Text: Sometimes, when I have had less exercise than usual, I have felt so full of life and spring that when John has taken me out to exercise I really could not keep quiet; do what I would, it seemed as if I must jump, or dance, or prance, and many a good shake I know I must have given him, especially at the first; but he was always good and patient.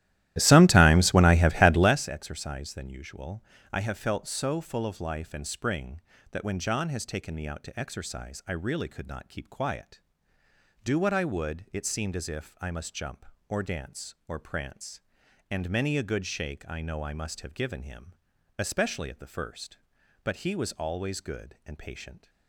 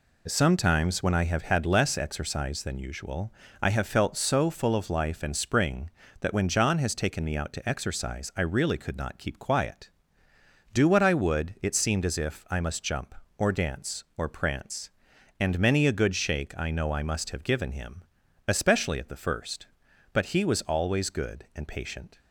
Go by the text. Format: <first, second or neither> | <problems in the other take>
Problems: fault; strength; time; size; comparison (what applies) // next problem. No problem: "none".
second | starts louder than the rest; strong; until 2.0 s; 14 dB